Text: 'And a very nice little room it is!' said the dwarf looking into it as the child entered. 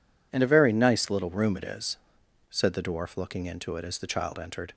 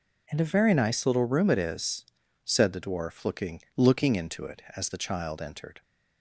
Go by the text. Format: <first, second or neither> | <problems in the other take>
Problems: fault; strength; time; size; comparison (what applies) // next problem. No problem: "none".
first | says "looking" twice; at 3.7 s